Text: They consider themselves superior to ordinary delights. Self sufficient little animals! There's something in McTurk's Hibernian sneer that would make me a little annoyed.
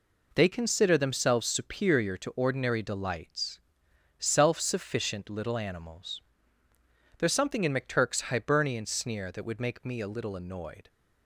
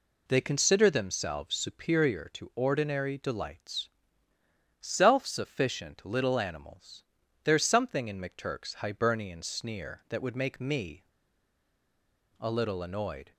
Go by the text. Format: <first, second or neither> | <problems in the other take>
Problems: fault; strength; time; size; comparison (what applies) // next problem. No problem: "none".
first | pauses between "me" and "a"; strong; at 11.0 s; 1.3 s long